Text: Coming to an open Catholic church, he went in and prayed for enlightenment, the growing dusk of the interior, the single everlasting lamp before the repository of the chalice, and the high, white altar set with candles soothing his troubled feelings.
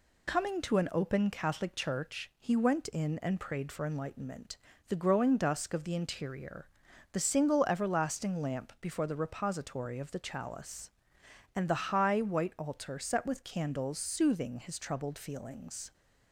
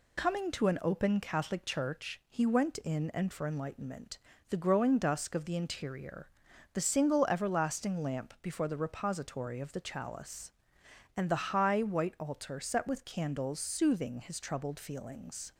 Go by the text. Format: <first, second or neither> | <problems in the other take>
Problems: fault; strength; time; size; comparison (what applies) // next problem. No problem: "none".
first | skips "prayed"; at 3.3 s